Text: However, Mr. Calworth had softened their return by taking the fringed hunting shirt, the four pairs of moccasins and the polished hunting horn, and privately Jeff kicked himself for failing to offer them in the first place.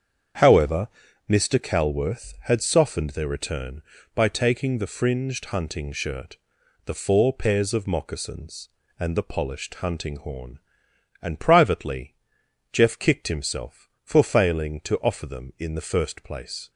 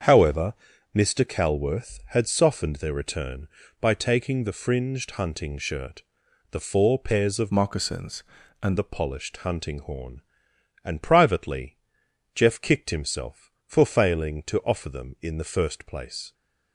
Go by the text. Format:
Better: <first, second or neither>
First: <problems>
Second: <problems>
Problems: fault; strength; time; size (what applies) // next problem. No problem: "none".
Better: first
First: starts louder than the rest; strong; until 1.7 s; 7.5 dB // pauses between "privately" and "Jeff"; noticeable; at 12.1 s; 0.56 s long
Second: starts louder than the rest; until 1.4 s; 7 dB // changes voice from "moccasins" to "and"; from 7.5 to 8.7 s; 1.2 s long // pauses between "privately" and "Jeff"; noticeable; at 11.7 s; 0.56 s long